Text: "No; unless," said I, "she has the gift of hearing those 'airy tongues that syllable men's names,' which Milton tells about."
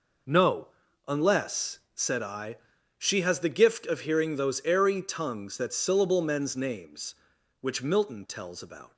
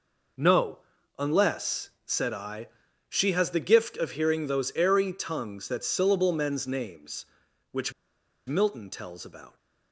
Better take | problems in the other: first | pauses between "which" and "Milton"; noticeable; at 7.9 s; 0.54 s long

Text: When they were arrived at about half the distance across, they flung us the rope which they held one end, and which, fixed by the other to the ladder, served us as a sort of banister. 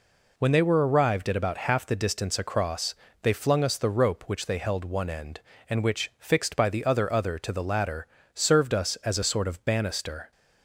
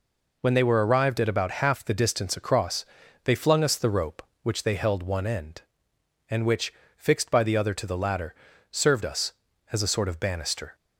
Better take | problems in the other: second | says "other" twice; at 7.0 s

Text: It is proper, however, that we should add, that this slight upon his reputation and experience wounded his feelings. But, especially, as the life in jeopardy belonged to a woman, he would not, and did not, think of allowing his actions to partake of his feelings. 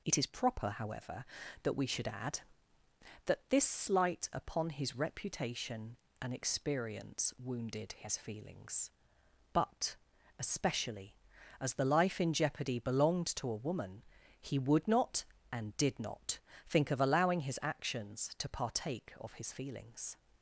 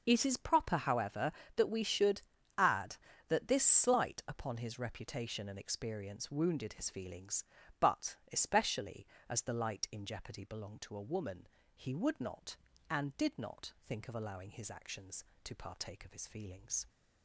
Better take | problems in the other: first | pauses between "should" and "add"; slight; at 2.2 s; 0.34 s long // says "light" for "life"; at 9.5 s

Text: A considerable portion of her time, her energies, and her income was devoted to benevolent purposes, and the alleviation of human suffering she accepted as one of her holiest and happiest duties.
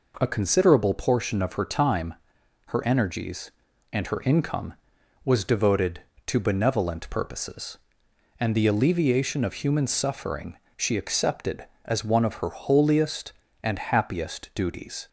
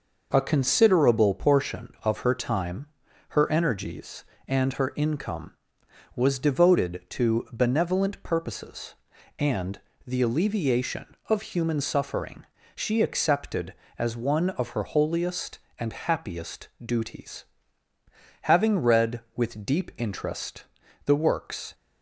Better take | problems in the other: first | pauses between "and" and "the"; slight; at 9.7 s; 0.30 s long // pauses between "suffering" and "she"; slight; at 12.4 s; 0.28 s long; slight in the first // goes on to say "Having read with deep interest the works"; strong; from 18.4 s on; 3.3 s long

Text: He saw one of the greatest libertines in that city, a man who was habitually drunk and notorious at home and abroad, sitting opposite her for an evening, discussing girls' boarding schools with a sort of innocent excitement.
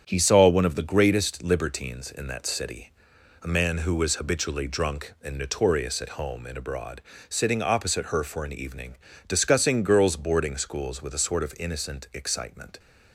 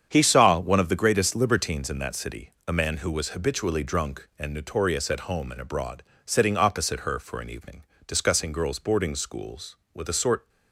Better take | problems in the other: first | starts louder than the rest; strong; until 1.1 s; 8 dB; strong in the first // stops before "of innocent excitement"; at 10.4 s

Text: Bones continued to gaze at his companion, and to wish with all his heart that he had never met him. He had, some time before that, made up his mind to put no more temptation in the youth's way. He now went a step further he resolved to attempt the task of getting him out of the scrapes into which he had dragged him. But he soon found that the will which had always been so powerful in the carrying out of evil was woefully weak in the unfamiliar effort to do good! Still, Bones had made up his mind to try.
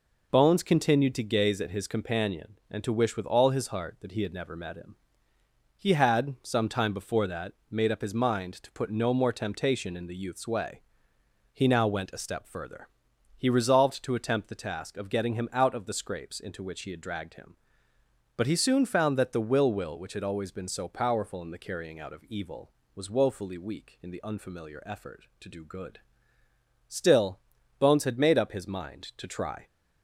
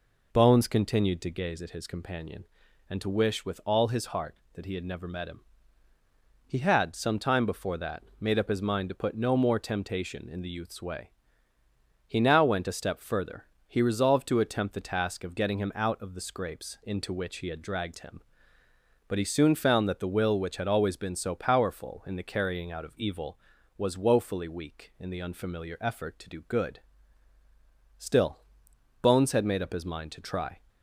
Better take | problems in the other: second | pauses between "further" and "he"; noticeable; at 12.8 s; 0.50 s long; slight in the second // says "will" twice; at 19.7 s

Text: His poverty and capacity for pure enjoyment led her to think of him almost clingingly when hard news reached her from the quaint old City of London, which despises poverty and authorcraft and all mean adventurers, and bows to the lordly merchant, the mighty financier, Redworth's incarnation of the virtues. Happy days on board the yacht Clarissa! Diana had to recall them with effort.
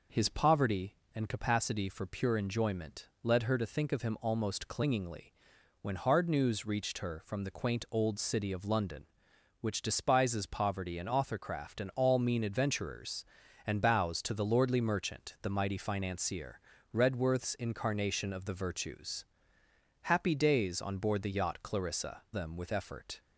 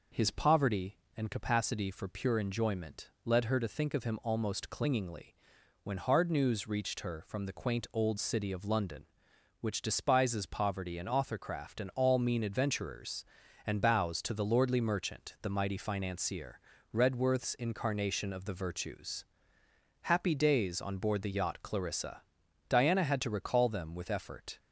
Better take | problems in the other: second | pauses between "enjoyment" and "led"; slight; at 3.0 s; 0.16 s long; slight in the second // pauses between "clingingly" and "when"; noticeable; at 5.3 s; 0.50 s long; noticeable in the second // skips "Diana had to recall"; at 22.2 s

